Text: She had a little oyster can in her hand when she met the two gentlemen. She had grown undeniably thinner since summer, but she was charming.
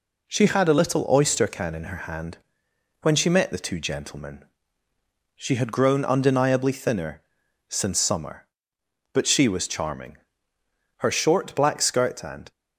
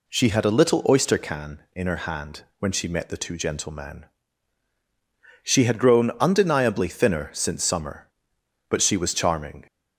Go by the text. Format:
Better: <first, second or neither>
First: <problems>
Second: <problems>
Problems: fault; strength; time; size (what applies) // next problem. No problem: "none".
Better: second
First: pauses between "hand" and "when"; noticeable; at 2.3 s; 0.66 s long // pauses between "thinner" and "since"; noticeable; at 7.2 s; 0.48 s long // goes on to say "Her short black skirt and"; from 10.9 s on; 1.5 s long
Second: none